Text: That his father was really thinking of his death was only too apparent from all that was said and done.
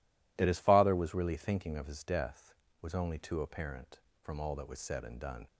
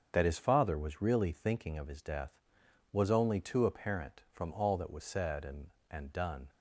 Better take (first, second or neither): first